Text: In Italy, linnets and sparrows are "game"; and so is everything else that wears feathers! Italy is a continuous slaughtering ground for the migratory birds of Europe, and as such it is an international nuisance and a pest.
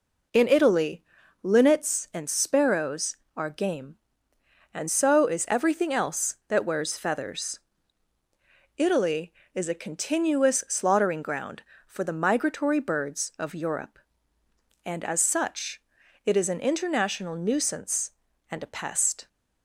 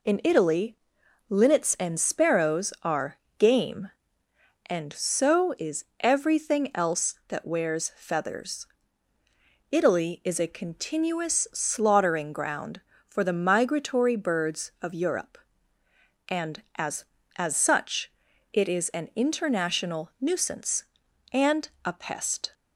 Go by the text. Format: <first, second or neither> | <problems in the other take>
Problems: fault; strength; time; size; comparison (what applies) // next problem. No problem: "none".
first | pauses between "are" and "game"; slight; at 3.1 s; 0.18 s long // pauses between "is" and "everything"; slight; at 5.8 s; 0.16 s long // says "as" twice; at 17.3 s // pauses between "such" and "it"; at 18.0 s; 0.44 s long; also in the first